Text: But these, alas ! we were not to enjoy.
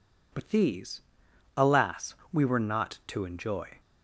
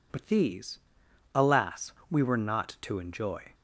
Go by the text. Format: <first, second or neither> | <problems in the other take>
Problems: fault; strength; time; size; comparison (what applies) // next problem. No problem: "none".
neither | none